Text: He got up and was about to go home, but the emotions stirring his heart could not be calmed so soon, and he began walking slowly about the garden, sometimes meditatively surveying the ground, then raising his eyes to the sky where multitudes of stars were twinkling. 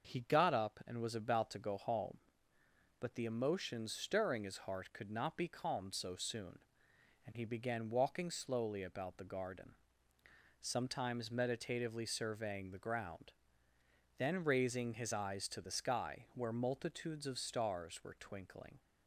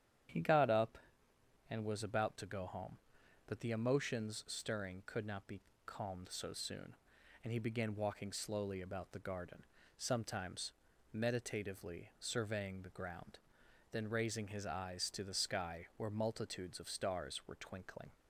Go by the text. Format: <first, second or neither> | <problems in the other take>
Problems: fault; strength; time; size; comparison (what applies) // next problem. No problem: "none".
first | starts louder than the rest; strong; until 2.0 s; 9.5 dB; also in the first // skips "his heart"; at 5.0 s // pauses between "be" and "calmed"; slight; at 5.6 s; 0.26 s long // pauses between "sometimes" and "meditatively"; at 10.7 s; 0.40 s long